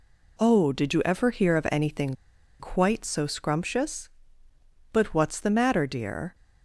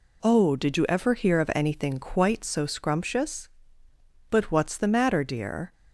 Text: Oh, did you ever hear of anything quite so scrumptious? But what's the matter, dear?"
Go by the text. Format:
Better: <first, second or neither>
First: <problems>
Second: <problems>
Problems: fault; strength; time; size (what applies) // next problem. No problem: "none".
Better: second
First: pauses between "anything" and "quite"; noticeable; at 2.1 s; 0.47 s long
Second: none